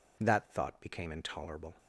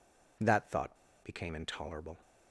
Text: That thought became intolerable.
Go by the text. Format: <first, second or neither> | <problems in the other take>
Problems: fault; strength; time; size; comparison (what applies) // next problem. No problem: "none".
first | pauses between "thought" and "became"; slight; at 0.9 s; 0.26 s long